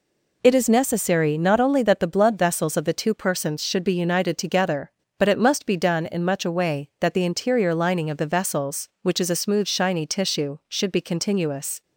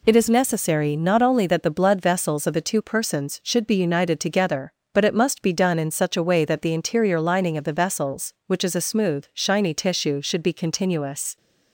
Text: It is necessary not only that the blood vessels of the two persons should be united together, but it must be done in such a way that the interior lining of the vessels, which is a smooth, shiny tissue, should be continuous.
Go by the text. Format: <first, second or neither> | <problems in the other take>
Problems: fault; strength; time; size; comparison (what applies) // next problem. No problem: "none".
second | says "much" for "such"; at 6.2 s